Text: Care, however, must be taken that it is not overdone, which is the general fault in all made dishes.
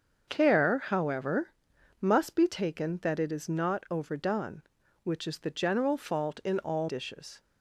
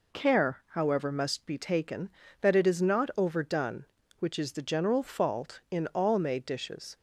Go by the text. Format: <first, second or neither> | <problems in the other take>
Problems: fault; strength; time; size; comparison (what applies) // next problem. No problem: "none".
second | starts louder than the rest; until 1.2 s; 6.5 dB // skips "made"; at 6.8 s